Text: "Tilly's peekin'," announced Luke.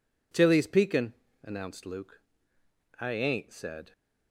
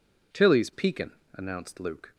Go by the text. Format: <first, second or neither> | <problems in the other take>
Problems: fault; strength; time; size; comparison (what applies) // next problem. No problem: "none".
second | goes on to say "I ain't said"; noticeable; from 3.0 s on; 0.92 s long